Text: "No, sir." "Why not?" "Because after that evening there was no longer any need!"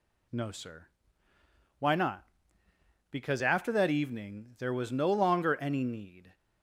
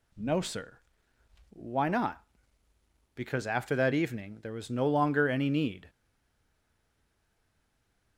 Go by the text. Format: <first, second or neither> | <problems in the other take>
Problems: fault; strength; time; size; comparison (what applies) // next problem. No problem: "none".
first | stays silent after the last word; from 5.8 s on; 2.3 s long